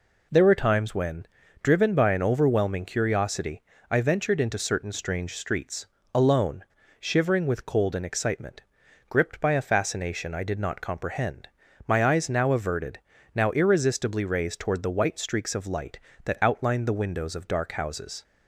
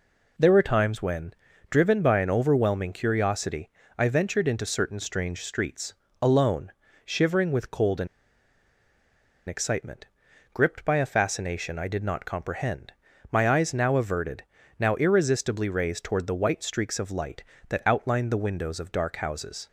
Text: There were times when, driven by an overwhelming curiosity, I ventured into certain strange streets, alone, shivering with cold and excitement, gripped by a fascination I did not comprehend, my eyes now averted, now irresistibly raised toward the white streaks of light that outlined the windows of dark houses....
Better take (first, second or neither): first